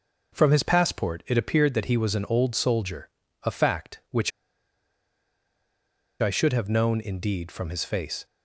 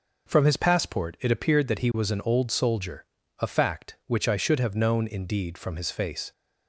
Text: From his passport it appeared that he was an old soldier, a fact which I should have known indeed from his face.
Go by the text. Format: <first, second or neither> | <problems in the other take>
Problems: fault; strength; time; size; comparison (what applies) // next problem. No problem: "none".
second | pauses between "which" and "I"; strong; at 4.3 s; 1.9 s long